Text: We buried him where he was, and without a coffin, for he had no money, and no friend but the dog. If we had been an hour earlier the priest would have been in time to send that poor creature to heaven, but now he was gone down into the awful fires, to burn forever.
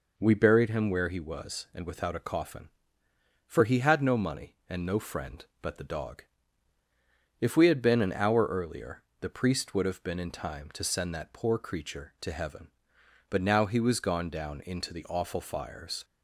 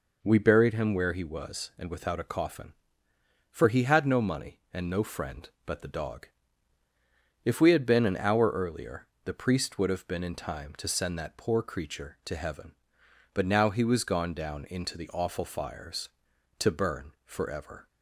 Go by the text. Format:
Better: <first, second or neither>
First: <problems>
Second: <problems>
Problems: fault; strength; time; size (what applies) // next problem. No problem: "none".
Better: second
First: pauses between "earlier" and "the"; slight; at 9.0 s; 0.18 s long // stops before "to burn forever"; at 16.0 s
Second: pauses between "earlier" and "the"; slight; at 9.0 s; 0.18 s long